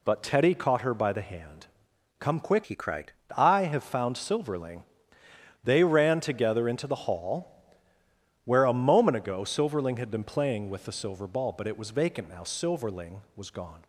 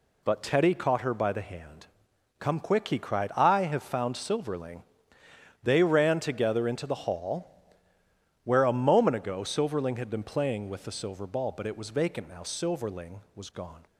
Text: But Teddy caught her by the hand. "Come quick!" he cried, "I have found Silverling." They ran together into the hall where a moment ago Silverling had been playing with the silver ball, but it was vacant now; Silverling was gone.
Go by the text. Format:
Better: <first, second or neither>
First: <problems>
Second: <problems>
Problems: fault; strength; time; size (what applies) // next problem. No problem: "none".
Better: second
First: changes voice from "he" to "cried"; from 2.6 to 3.1 s; 0.5 s long // pauses between "hall" and "where"; noticeable; at 7.4 s; 0.96 s long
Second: pauses between "hall" and "where"; noticeable; at 7.4 s; 0.96 s long